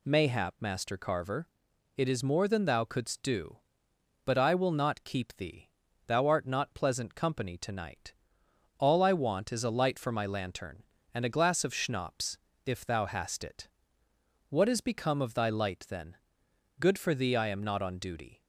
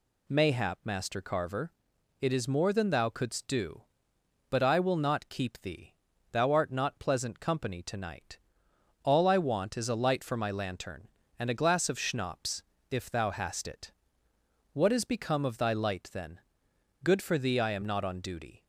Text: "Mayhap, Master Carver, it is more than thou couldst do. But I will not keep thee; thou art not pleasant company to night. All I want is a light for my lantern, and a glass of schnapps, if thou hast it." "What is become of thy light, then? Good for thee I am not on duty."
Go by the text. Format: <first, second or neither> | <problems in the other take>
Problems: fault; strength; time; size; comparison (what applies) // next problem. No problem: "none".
neither | none